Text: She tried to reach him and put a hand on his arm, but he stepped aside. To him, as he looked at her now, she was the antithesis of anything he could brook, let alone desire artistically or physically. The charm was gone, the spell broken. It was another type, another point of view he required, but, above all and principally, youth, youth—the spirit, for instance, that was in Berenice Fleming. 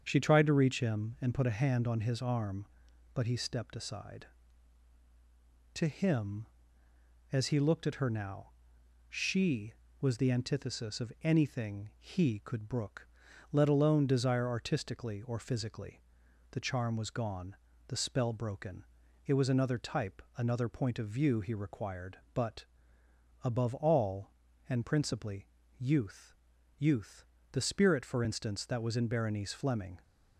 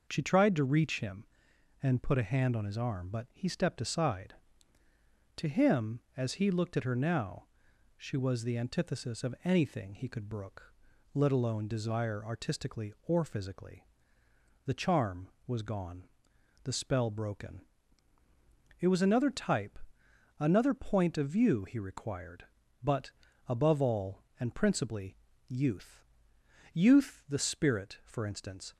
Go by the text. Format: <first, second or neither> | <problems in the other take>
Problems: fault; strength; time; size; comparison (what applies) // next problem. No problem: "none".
first | starts louder than the rest; noticeable; until 1.0 s; 6 dB; strong in the first // stops before "that was in Berenice Fleming"; at 28.7 s